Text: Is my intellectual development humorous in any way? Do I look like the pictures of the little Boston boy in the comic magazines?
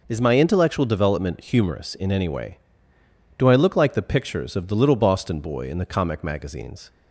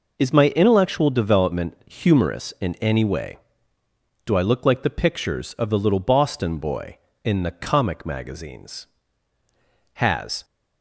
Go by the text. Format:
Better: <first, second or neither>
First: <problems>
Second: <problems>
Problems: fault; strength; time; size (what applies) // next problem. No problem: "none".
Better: first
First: none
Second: goes on to say "Has"; from 9.9 s on; 0.50 s long